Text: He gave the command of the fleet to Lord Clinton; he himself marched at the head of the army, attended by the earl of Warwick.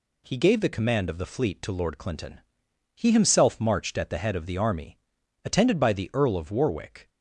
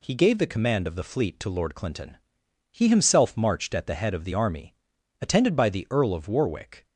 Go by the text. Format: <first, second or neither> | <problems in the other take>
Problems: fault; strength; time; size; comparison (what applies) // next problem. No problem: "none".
neither | none